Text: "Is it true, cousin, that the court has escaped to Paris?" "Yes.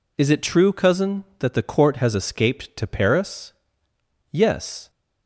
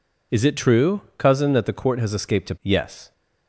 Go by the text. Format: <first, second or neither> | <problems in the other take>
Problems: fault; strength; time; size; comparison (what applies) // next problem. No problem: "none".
first | skips "Paris"; at 2.5 s